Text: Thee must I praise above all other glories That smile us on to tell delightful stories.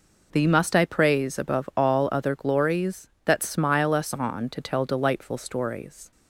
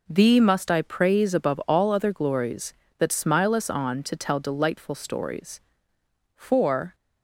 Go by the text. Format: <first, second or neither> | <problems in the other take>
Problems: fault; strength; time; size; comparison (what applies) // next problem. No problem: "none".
first | goes on to say "For"; from 6.3 s on; 0.58 s long